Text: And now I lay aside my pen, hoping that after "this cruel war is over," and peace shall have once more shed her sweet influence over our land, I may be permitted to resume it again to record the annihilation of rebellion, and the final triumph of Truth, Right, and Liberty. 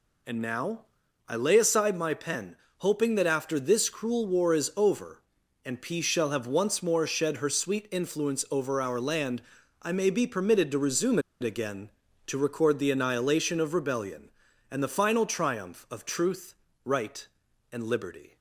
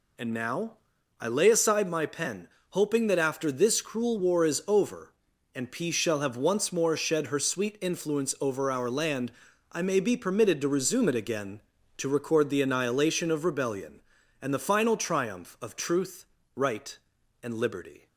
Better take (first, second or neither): second